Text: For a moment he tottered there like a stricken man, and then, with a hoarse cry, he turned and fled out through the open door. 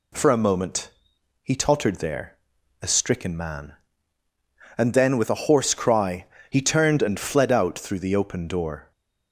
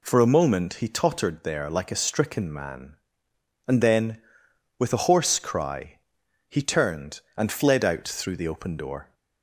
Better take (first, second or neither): second